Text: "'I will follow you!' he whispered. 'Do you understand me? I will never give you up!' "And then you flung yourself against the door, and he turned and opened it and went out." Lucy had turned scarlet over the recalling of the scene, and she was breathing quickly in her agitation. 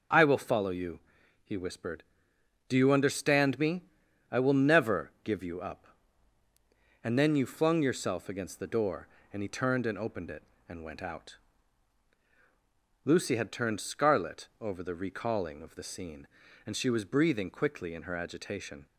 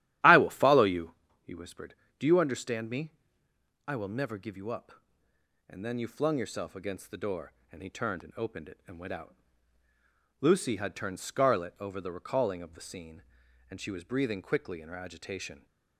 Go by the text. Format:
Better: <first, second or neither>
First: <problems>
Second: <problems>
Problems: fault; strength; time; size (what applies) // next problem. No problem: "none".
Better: first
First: none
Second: starts louder than the rest; strong; until 1.2 s; 12.5 dB